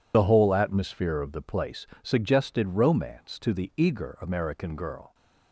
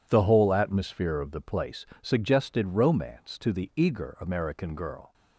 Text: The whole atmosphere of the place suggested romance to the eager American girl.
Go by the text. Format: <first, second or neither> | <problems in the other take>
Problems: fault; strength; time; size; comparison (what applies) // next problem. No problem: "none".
second | loses the start of "The"; at 0.1 s; 45 ms // pauses between "place" and "suggested"; slight; at 1.8 s; 0.16 s long; slight in the second